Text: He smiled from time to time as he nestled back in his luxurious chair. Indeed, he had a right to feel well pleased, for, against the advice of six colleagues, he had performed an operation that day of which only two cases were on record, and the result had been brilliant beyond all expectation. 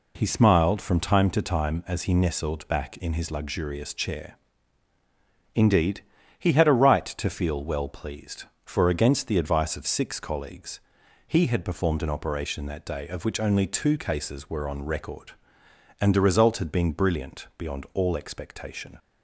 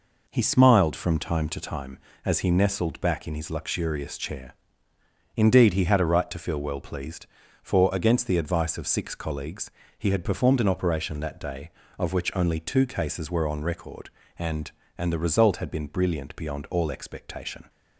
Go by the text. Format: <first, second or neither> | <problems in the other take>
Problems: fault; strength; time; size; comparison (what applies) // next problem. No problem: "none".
first | says "and" twice; at 14.9 s